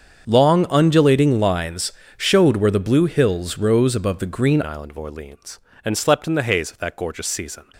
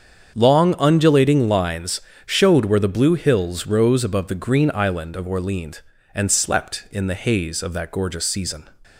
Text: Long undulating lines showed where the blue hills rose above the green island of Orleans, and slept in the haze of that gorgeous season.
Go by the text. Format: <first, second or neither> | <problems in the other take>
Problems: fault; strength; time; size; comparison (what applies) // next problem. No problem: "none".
second | starts louder than the rest; until 1.3 s; 7 dB; strong in the second // pauses between "lines" and "showed"; slight; at 1.9 s; 0.24 s long; slight in the second // changes voice at "island"; from 4.6 s on; 3.0 s long